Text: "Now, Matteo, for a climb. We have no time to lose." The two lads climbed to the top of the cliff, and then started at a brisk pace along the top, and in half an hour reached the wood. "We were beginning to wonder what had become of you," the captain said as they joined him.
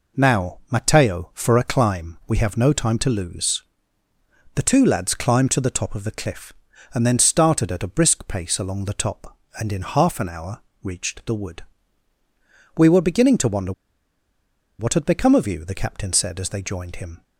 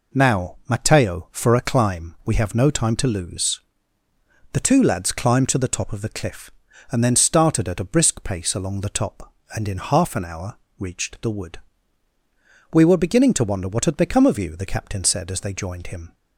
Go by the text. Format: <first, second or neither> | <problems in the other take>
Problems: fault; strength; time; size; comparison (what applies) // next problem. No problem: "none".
second | pauses between "hour" and "reached"; slight; at 10.5 s; 0.24 s long; slight in the second // pauses between "wonder" and "what"; at 13.7 s; 1.0 s long